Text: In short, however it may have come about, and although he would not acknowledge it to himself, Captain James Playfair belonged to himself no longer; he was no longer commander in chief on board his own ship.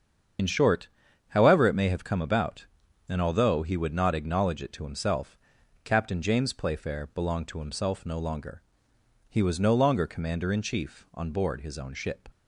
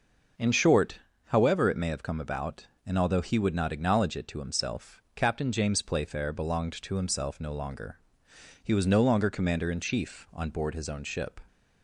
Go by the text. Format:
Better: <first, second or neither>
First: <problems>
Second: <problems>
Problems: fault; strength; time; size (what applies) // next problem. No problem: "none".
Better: second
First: loses the start of "In"; at 0.3 s; 45 ms // starts louder than the rest; strong; until 1.8 s; 7.5 dB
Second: none